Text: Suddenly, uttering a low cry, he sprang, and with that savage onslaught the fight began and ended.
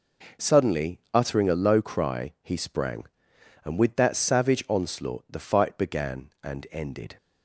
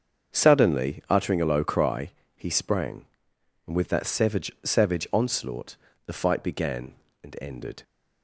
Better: first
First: none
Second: starts louder than the rest; until 1.3 s; 7 dB // says "savage" twice; at 4.6 s // pauses between "onslaught" and "the"; slight; at 5.7 s; 0.32 s long

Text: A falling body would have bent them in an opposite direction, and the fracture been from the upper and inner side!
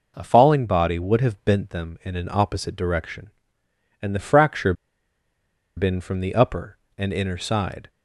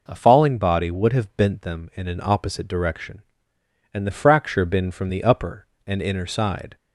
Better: second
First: pauses between "fracture" and "been"; at 4.7 s; 1.0 s long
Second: none

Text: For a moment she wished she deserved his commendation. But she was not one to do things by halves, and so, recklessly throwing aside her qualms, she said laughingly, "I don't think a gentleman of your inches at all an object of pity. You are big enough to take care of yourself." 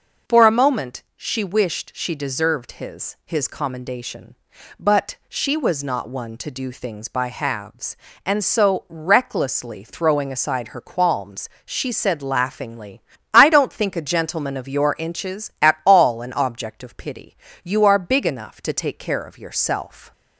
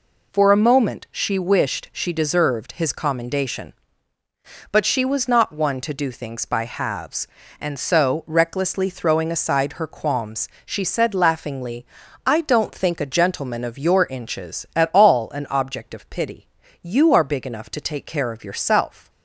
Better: second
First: says "his" twice; at 3.2 s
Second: none

